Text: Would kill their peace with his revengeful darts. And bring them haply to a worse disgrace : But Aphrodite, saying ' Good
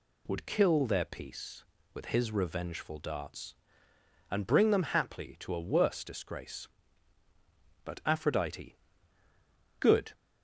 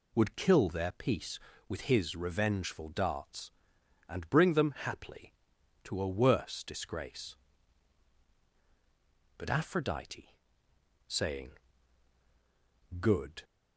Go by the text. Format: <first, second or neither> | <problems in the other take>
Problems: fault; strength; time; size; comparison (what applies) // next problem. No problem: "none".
second | skips "saying"; at 9.0 s